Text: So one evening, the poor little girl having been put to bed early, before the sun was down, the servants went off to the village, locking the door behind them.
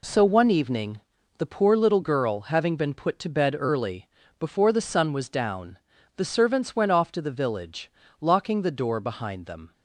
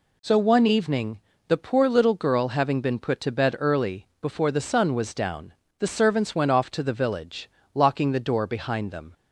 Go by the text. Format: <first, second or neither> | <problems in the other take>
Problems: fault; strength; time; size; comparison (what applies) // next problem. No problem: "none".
neither | none